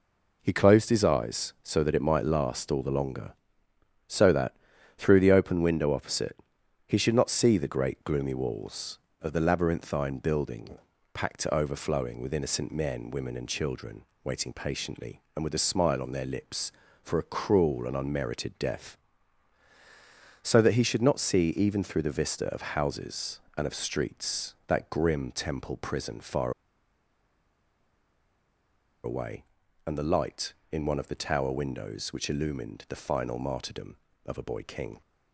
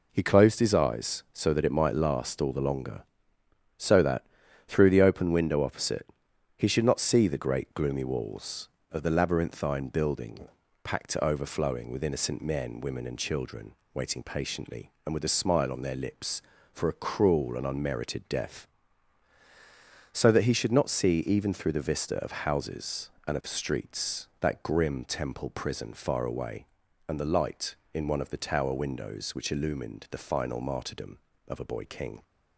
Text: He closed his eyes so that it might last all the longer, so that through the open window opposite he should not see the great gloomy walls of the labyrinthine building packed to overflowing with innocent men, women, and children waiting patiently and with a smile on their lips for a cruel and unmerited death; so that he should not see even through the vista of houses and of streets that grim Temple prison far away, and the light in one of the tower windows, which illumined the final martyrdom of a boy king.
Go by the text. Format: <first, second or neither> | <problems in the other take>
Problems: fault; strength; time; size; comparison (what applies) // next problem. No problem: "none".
second | pauses between "that" and "through"; at 4.5 s; 0.42 s long; also in the second // pauses between "opposite" and "he"; noticeable; at 6.3 s; 0.52 s long; noticeable in the second // pauses between "building" and "packed"; slight; at 10.7 s; 0.36 s long; slight in the second // pauses between "children" and "waiting"; slight; at 14.0 s; 0.20 s long; slight in the second // pauses between "far" and "away"; strong; at 26.5 s; 2.5 s long